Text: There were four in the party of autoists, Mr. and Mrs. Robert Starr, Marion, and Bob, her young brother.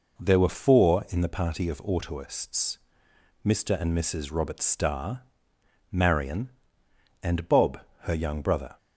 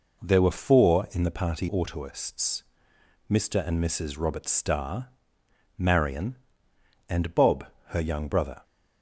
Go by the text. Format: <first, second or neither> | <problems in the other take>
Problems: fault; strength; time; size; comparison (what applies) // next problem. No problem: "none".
first | skips "of"; at 1.6 s